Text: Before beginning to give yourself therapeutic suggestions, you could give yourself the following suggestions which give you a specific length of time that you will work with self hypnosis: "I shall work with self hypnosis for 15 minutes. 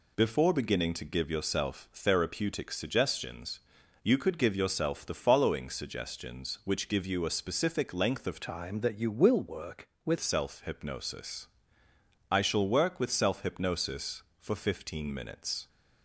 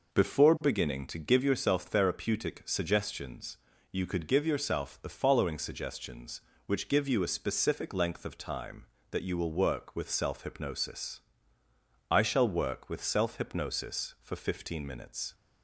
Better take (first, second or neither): second